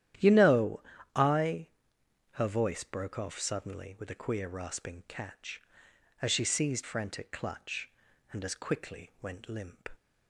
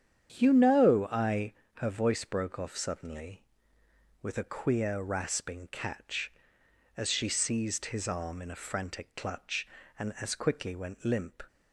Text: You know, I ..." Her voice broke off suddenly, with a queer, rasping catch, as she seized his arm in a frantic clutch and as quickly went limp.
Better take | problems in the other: second | starts louder than the rest; strong; until 1.5 s; 11.5 dB; strong in the second // skips "his arm in a"; at 6.8 s

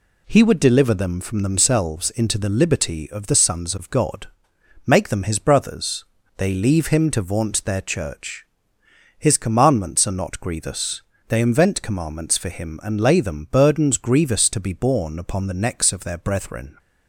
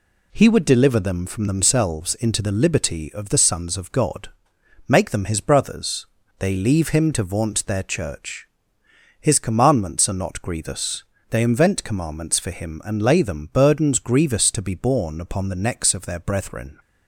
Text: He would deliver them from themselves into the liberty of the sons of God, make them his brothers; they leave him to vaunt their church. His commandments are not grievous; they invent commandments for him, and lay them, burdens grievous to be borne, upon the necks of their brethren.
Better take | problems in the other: neither | none

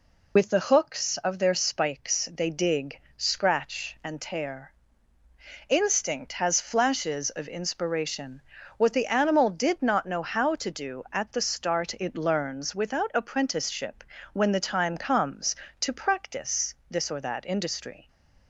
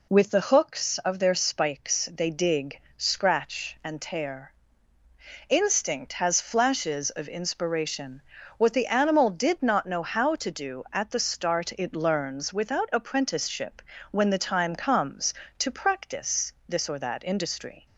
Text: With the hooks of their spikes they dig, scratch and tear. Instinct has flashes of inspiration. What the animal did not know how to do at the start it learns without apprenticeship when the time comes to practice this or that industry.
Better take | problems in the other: second | loses the start of "With"; at 0.3 s; 60 ms // pauses between "apprenticeship" and "when"; slight; at 14.0 s; 0.28 s long; slight in the second // pauses between "practice" and "this"; slight; at 16.7 s; 0.16 s long; slight in the second

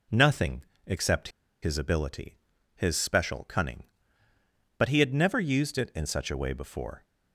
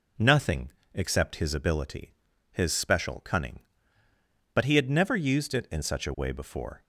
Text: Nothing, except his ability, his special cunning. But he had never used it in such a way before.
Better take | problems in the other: second | pauses between "except" and "his"; slight; at 1.2 s; 0.33 s long

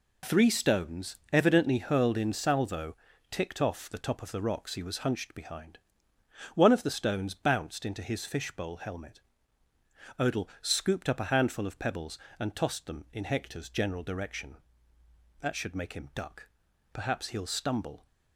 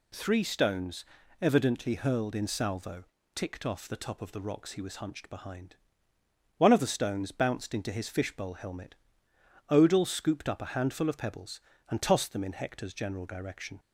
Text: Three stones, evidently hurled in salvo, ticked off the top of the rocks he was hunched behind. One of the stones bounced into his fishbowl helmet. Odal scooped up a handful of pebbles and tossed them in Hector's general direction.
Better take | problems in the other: second | goes on to say "That should make him duck Perhaps he'll stumble"; strong; from 15.4 s on; 2.6 s long

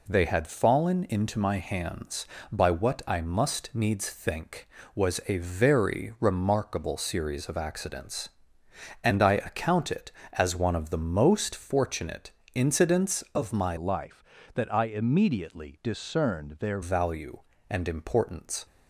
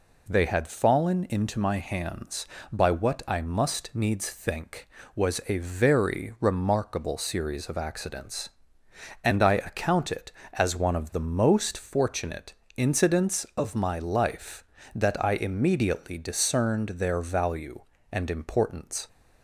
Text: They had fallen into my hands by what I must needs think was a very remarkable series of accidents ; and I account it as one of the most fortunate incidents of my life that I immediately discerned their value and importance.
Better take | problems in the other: second | pauses between "fortunate" and "incidents"; slight; at 12.3 s; 0.24 s long; slight in the second // changes voice from "life" to "their"; from 13.7 to 16.7 s; 3.0 s long

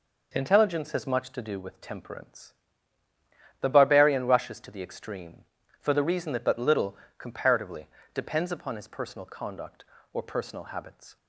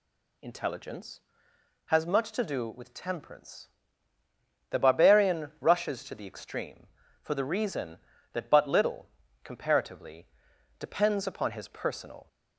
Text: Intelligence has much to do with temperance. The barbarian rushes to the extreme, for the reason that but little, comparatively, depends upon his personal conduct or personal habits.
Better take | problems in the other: first | stops before "conduct or personal habits"; at 12.2 s

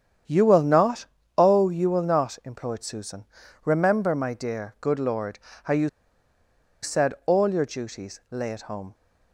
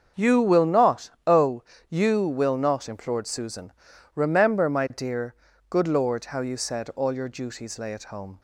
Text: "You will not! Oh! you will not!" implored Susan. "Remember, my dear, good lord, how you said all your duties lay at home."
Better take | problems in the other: second | starts louder than the rest; strong; until 1.5 s; 8.5 dB; also in the second // pauses between "you" and "said"; noticeable; at 5.8 s; 0.94 s long

